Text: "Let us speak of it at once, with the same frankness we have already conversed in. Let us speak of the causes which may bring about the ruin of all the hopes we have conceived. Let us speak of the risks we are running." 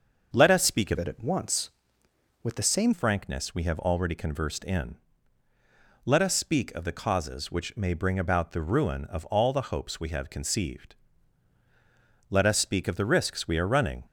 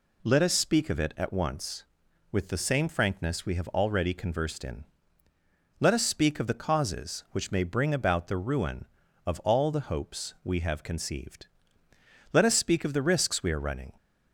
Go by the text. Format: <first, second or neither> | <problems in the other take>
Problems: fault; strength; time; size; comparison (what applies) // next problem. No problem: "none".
second | starts louder than the rest; until 1.3 s; 6.5 dB // changes voice from "it" to "same"; from 0.9 to 2.9 s; 2.0 s long